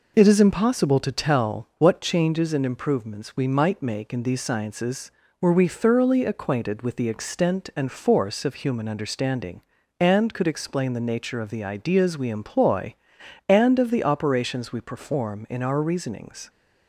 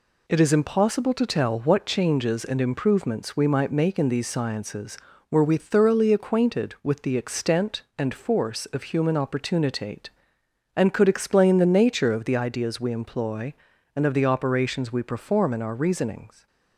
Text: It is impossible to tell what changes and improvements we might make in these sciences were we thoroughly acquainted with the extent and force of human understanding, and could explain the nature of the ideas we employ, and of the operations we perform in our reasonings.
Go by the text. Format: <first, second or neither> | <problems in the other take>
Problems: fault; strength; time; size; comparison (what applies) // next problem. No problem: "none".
first | says "opportunitate" for "understanding"; at 9.1 s